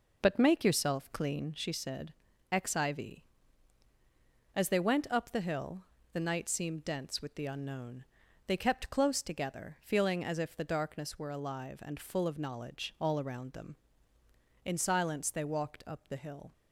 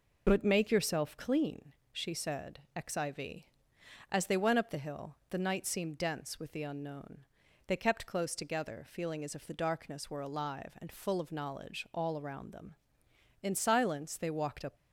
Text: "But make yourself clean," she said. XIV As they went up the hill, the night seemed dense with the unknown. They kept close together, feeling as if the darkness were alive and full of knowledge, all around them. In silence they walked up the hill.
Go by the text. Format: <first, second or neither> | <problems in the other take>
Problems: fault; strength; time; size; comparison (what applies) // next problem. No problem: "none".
first | stops before "the hill"; at 14.7 s